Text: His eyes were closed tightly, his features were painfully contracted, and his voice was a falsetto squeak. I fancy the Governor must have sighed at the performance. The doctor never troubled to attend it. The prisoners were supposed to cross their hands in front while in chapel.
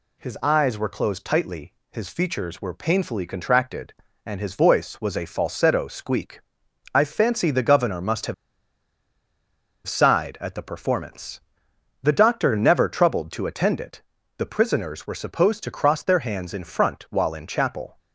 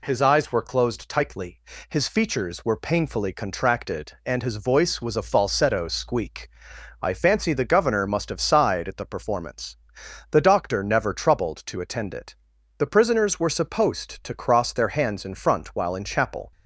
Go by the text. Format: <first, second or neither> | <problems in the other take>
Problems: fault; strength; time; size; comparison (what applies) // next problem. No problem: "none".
second | pauses between "have" and "sighed"; strong; at 8.3 s; 1.5 s long